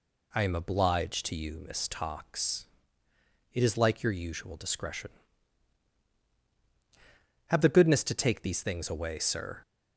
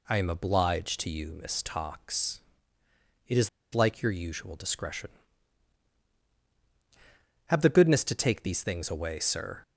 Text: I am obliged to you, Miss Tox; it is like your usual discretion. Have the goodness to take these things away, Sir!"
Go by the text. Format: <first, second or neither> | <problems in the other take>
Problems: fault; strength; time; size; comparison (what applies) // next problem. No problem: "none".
first | pauses between "is" and "like"; slight; at 3.4 s; 0.25 s long